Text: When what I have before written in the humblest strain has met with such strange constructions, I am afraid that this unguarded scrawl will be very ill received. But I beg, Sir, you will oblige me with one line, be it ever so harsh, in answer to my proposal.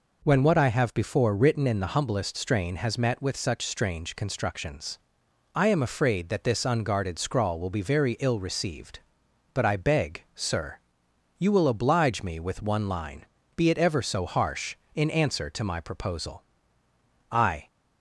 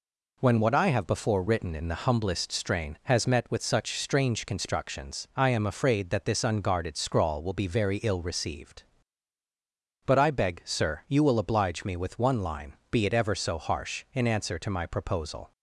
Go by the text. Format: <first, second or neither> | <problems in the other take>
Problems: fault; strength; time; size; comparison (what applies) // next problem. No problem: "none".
second | goes on to say "I"; slight; from 17.2 s on; 0.36 s long